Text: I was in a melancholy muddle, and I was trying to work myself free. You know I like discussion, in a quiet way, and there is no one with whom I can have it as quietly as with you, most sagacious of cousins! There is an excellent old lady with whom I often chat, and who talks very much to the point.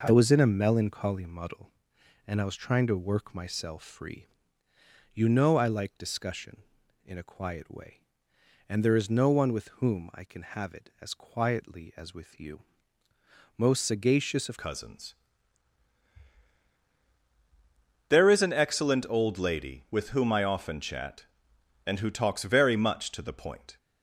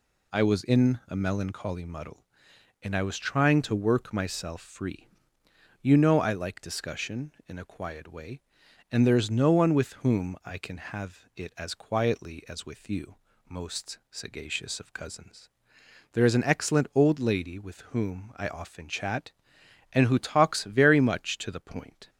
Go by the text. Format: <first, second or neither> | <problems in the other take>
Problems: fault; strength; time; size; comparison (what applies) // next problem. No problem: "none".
second | changes voice at "cousins"; from 14.5 s on; 9.2 s long